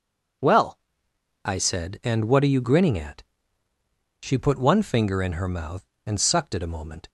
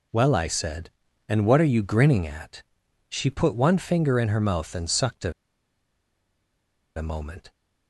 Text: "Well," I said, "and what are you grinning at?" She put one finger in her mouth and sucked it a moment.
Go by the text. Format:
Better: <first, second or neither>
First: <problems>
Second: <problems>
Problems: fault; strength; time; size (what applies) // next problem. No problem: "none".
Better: first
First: none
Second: pauses between "it" and "a"; strong; at 5.3 s; 1.6 s long